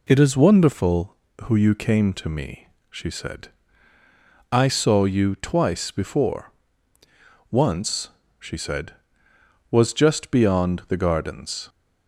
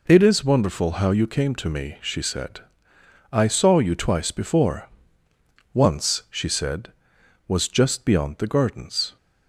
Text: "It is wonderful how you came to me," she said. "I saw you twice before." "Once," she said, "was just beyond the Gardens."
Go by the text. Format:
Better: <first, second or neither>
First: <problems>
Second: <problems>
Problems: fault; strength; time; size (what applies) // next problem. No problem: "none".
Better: second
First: says "who" for "how"; at 1.4 s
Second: none